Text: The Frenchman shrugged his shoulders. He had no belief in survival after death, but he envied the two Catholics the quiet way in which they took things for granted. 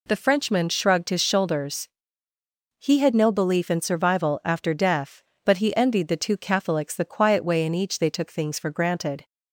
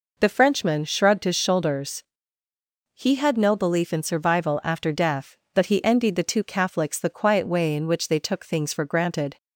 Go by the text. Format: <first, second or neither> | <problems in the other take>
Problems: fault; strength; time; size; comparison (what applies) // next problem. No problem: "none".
second | says "each" for "which"; at 7.7 s